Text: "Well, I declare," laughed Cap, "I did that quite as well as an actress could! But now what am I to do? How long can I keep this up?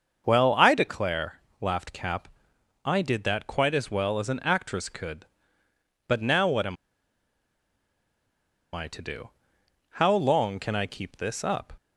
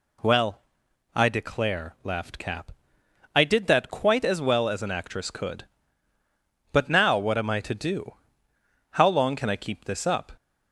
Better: second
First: starts louder than the rest; until 1.2 s; 6.5 dB // pauses between "am" and "I"; strong; at 6.7 s; 1.9 s long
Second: none

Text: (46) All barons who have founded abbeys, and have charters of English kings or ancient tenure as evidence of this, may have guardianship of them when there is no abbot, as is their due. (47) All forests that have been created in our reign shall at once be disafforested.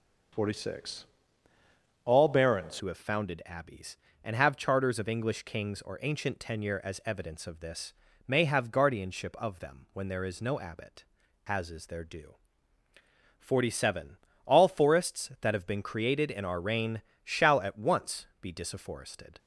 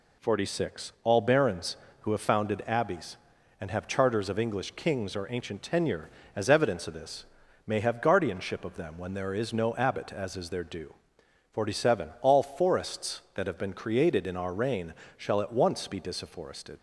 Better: second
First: changes voice at "who"; from 2.7 s on; 16.6 s long // pauses between "reign" and "shall"; slight; at 16.9 s; 0.24 s long // pauses between "once" and "be"; slight; at 18.2 s; 0.16 s long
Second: pauses between "reign" and "shall"; slight; at 14.9 s; 0.24 s long

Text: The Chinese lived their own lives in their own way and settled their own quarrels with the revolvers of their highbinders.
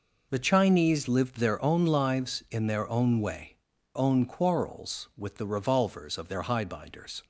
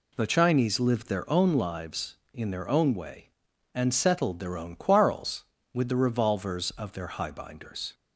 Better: second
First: skips "and settled their"; at 3.7 s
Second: none

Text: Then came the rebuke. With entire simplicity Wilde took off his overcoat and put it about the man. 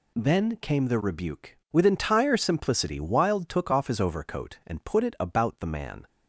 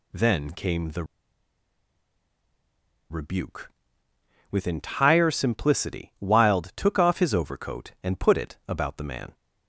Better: first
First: none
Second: pauses between "the" and "rebuke"; strong; at 1.0 s; 2.0 s long

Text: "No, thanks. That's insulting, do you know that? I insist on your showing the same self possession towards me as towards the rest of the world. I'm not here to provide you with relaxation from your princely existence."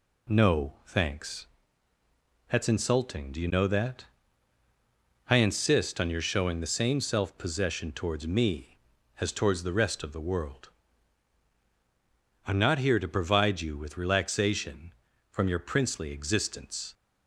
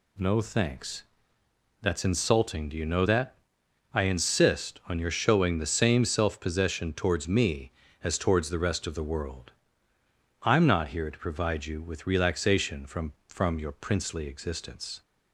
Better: first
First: none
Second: says "from" twice; at 13.2 s

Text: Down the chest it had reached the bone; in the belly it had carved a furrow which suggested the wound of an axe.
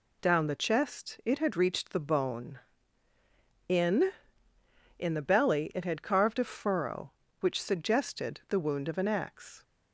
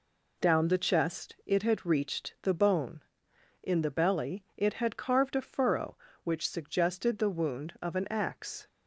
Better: second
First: says "in" twice; at 4.9 s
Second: none

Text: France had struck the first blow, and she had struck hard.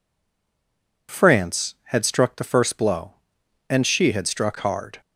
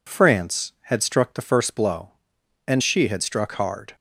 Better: second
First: stays silent before the first word; until 1.0 s; 1.0 s long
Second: none

